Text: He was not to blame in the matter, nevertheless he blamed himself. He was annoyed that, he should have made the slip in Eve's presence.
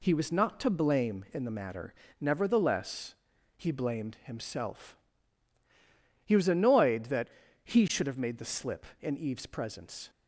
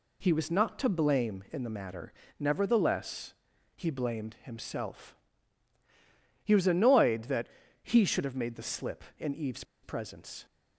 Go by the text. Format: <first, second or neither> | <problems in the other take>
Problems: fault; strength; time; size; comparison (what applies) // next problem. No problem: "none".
first | pauses between "nevertheless" and "he"; at 3.3 s; 0.42 s long; also in the first // pauses between "Eve's" and "presence"; slight; at 9.6 s; 0.19 s long